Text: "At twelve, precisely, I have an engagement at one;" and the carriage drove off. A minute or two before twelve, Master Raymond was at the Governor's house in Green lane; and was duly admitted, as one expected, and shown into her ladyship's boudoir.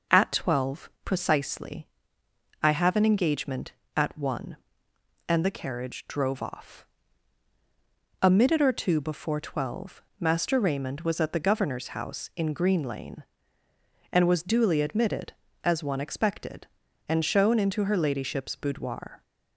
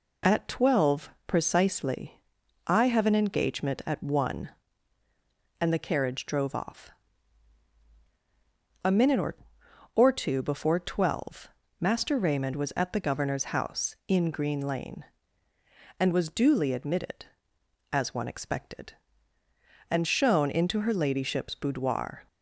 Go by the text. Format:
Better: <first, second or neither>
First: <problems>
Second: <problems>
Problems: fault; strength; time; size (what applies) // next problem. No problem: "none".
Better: first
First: none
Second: says "or" twice; at 9.9 s